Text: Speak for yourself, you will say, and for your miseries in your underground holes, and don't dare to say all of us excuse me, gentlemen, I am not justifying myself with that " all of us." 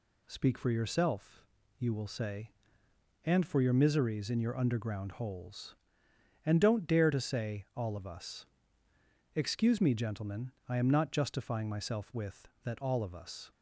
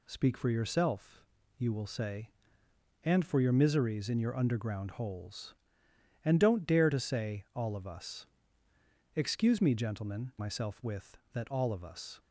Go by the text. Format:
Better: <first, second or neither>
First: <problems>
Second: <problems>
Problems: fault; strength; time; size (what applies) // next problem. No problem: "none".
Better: first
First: pauses between "us" and "excuse"; noticeable; at 8.4 s; 0.90 s long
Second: pauses between "us" and "excuse"; noticeable; at 8.2 s; 0.90 s long // skips "I am not justifying"; at 10.3 s